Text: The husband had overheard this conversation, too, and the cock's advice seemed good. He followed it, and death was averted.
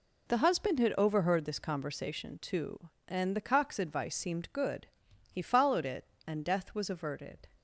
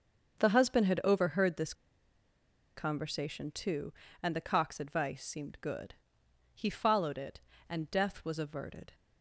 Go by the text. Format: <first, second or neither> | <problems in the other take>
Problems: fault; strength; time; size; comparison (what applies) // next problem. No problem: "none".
first | starts louder than the rest; until 1.4 s; 6.5 dB // pauses between "this" and "conversation"; at 1.7 s; 1.0 s long